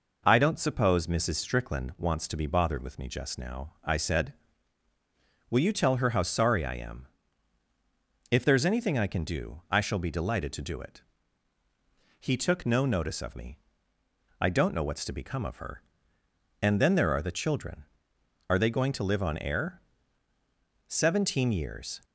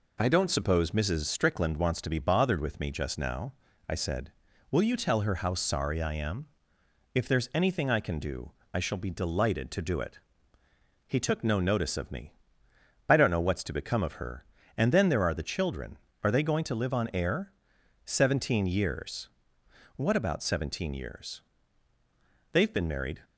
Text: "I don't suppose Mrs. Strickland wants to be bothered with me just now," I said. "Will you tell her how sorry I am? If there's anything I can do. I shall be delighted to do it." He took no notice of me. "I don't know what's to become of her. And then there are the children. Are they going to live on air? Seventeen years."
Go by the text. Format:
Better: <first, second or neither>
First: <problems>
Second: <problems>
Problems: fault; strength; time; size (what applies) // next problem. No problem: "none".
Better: first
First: none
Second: goes on to say "What about seventeen years They've been married"; strong; from 19.9 s on; 3.2 s long